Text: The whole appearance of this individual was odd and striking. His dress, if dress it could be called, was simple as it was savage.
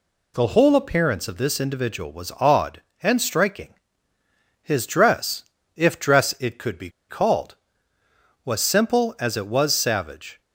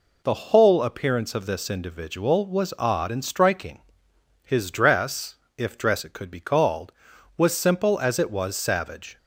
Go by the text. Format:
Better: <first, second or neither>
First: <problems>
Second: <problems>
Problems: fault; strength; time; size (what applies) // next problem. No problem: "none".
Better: second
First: pauses between "be" and "called"; slight; at 6.8 s; 0.20 s long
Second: none